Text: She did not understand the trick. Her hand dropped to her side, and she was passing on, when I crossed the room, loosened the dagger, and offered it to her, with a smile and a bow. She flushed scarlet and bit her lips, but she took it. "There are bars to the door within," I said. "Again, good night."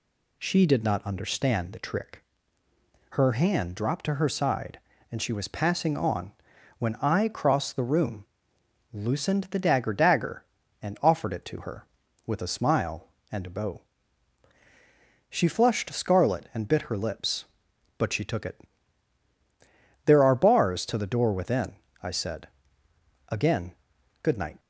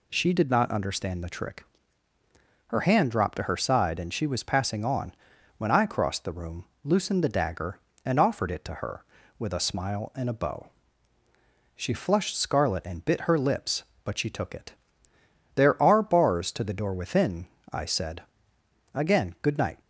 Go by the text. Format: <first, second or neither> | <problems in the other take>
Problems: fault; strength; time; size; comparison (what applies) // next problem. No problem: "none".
second | says "dagger" twice; at 9.9 s